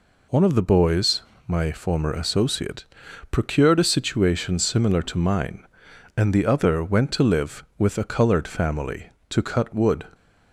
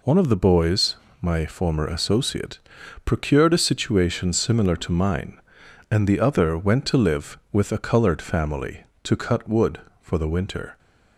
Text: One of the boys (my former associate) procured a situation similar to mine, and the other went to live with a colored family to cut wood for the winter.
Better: second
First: stops before "for the winter"; at 10.1 s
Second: none

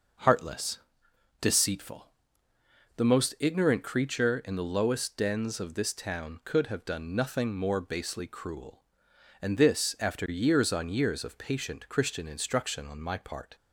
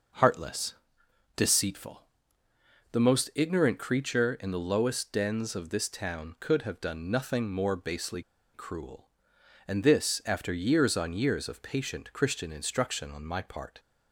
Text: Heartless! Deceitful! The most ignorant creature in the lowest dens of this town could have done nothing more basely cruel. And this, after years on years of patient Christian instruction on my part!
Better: first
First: none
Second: pauses between "basely" and "cruel"; slight; at 8.2 s; 0.32 s long

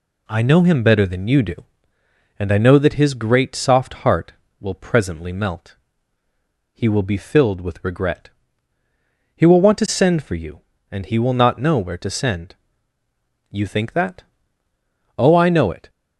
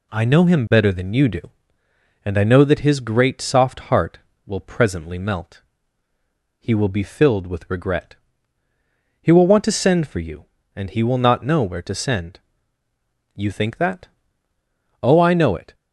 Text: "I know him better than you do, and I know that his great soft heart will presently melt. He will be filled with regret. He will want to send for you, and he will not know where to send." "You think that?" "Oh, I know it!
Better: neither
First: none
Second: none

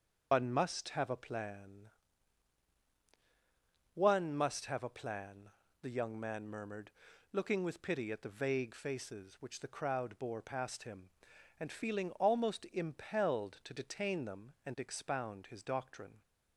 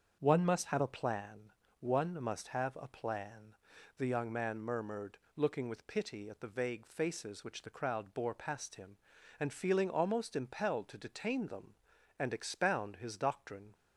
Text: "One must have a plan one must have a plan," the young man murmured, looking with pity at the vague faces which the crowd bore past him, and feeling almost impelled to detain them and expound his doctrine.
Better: second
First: loses the start of "One"; at 0.3 s; 105 ms // starts louder than the rest; until 1.3 s; 6.5 dB // pauses between "plan" and "one"; strong; at 1.9 s; 2.0 s long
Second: starts louder than the rest; until 1.2 s; 7 dB // pauses between "plan" and "one"; slight; at 1.5 s; 0.28 s long

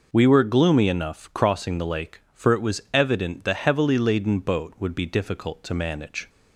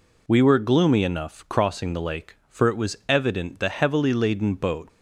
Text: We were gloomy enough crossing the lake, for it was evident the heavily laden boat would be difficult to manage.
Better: first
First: none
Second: stops before "would be difficult to manage"; at 4.8 s

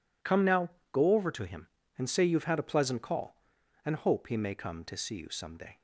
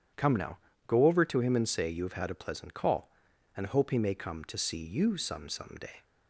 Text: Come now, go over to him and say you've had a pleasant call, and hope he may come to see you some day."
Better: first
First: none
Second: starts louder than the rest; strong; until 1.4 s; 8.5 dB // says "some" twice; at 5.4 s

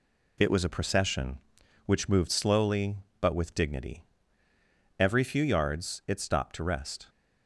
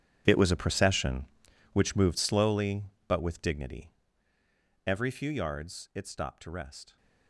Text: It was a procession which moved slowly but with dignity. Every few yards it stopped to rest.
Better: first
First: none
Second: gets quieter; strong; throughout; 16.5 dB

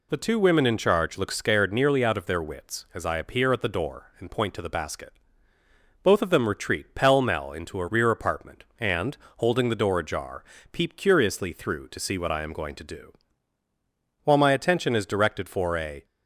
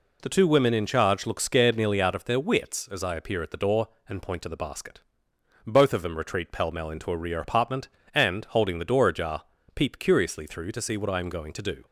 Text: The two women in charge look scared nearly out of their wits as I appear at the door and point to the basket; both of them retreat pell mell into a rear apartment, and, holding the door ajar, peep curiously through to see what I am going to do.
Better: second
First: goes on to say "While my attention is directed for a"; strong; from 14.2 s on; 1.8 s long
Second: none

